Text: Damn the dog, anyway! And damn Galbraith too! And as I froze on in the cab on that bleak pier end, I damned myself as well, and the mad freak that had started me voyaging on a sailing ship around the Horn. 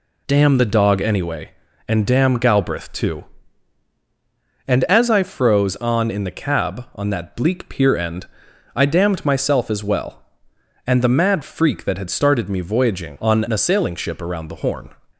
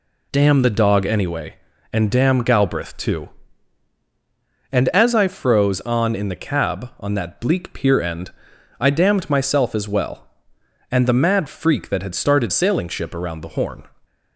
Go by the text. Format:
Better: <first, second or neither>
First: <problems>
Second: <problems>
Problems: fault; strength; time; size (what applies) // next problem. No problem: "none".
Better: first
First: none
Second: skips "me voyaging on a"; at 12.5 s